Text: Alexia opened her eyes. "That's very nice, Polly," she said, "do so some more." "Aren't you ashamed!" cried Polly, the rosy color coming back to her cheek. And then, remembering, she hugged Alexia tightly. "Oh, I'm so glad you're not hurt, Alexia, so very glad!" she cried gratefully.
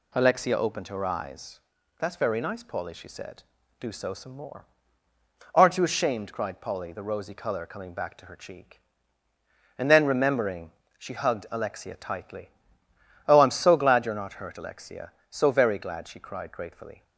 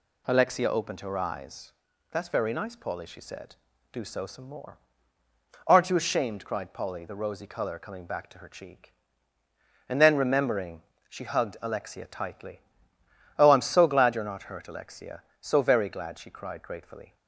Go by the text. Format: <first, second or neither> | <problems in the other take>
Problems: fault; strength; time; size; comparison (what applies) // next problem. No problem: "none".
neither | none